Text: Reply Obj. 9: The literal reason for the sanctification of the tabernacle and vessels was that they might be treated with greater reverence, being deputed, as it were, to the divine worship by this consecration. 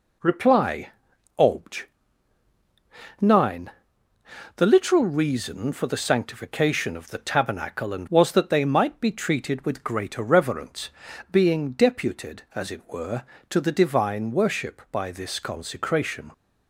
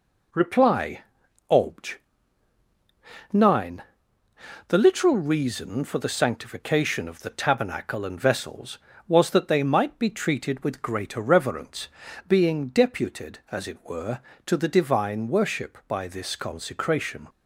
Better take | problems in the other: second | pauses between "Reply" and "Obj"; noticeable; at 0.8 s; 0.48 s long; noticeable in the second // skips "vessels"; at 8.0 s

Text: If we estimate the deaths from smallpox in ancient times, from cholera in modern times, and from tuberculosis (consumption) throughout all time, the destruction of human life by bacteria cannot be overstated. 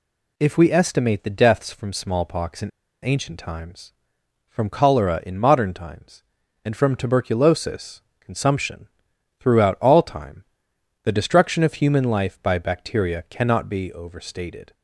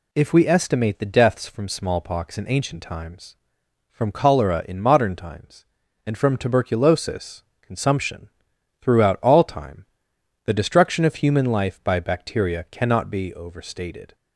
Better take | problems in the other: second | pauses between "in" and "ancient"; at 2.6 s; 0.36 s long

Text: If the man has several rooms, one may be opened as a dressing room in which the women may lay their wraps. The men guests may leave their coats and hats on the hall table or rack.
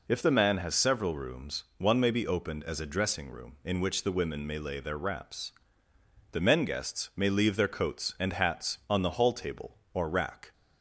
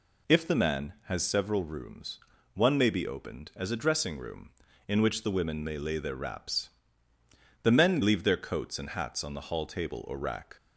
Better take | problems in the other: first | skips "guests may"; at 8.0 s

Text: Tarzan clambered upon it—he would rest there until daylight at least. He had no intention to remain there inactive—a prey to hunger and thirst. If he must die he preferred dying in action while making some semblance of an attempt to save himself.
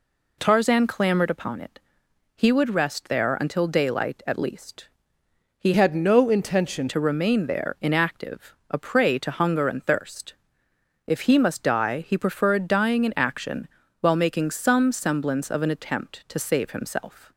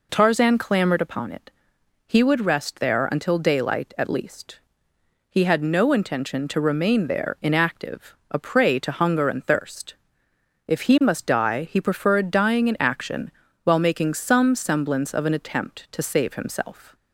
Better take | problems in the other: second | changes voice from "had" to "intention"; from 5.7 to 6.8 s; 1.1 s long // pauses between "action" and "while"; slight; at 13.6 s; 0.32 s long; slight in the second

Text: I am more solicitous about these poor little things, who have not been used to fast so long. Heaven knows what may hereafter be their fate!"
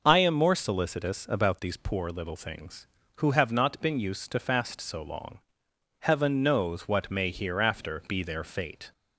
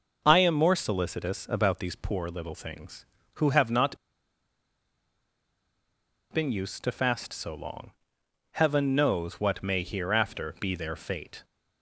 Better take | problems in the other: first | pauses between "not" and "been"; strong; at 3.9 s; 2.3 s long

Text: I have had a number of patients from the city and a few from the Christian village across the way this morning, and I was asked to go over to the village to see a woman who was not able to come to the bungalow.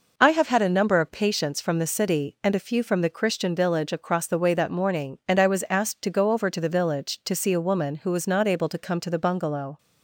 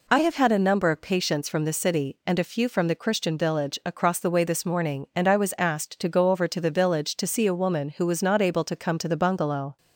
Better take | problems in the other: second | says "that" for "this"; at 4.5 s

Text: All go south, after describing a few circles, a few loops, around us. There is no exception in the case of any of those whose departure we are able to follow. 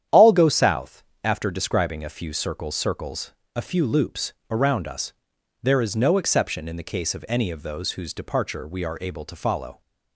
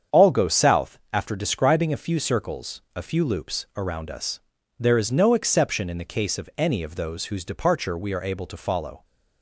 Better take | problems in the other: second | starts louder than the rest; strong; until 1.2 s; 9.5 dB; strong in the second // says "circles" twice; at 2.7 s

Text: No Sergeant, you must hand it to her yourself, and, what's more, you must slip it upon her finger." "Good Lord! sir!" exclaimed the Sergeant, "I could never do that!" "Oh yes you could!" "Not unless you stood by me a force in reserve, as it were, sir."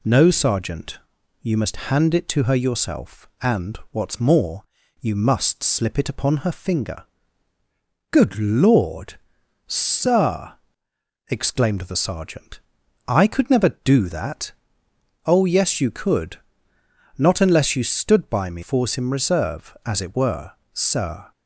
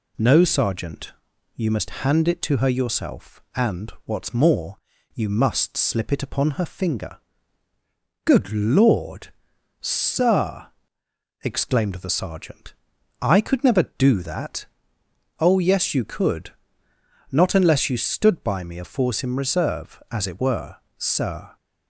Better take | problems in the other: second | skips "a"; at 18.6 s

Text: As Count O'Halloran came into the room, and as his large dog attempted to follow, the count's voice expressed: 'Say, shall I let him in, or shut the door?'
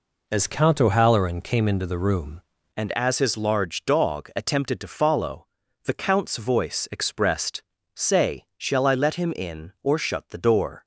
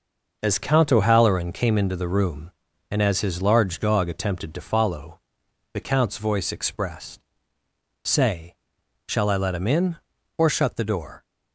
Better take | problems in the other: second | changes voice at "and"; from 2.7 s on; 8.1 s long

